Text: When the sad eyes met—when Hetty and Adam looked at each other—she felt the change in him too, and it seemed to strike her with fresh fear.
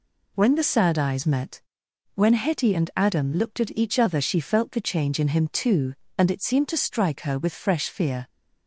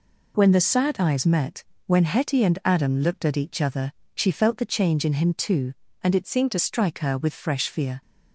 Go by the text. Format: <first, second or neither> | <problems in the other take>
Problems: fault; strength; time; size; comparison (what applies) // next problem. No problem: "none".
first | changes voice from "seemed" to "to"; from 6.2 to 6.5 s; 0.3 s long